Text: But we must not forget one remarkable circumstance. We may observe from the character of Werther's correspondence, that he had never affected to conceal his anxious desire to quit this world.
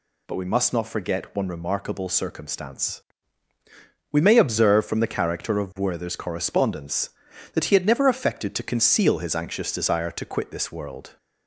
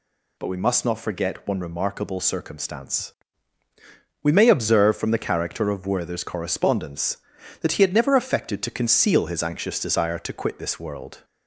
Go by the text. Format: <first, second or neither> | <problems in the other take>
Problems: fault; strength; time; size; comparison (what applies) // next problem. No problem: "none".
neither | none